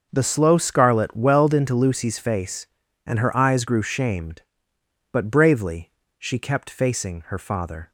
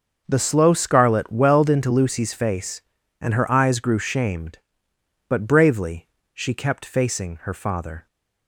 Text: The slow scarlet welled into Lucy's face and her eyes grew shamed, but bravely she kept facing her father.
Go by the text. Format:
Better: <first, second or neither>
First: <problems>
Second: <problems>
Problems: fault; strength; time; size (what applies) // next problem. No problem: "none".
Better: neither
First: starts louder than the rest; until 1.1 s; 6.5 dB // pauses between "bravely" and "she"; slight; at 5.9 s; 0.26 s long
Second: starts louder than the rest; until 1.2 s; 6.5 dB // pauses between "bravely" and "she"; slight; at 6.0 s; 0.26 s long